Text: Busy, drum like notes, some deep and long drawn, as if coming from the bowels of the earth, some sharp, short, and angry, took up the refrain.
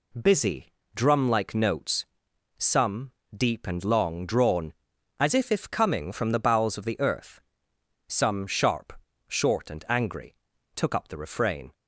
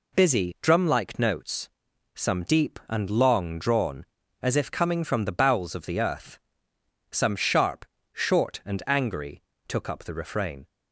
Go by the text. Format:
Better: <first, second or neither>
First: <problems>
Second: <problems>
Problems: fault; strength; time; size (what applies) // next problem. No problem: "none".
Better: second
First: pauses between "some" and "deep"; slight; at 3.1 s; 0.22 s long // says "if" twice; at 5.5 s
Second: none